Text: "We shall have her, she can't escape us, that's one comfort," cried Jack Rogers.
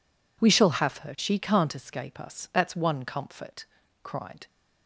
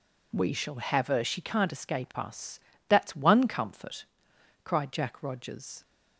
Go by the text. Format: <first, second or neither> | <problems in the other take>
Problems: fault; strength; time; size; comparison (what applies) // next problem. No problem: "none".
second | stops before "Jack Rogers"; at 4.4 s